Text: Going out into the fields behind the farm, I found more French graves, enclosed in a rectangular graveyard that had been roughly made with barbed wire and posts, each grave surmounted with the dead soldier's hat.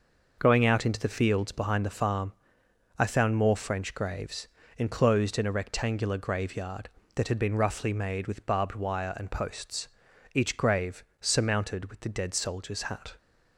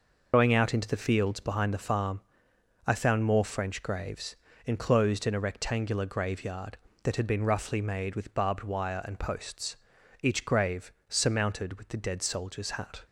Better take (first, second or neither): first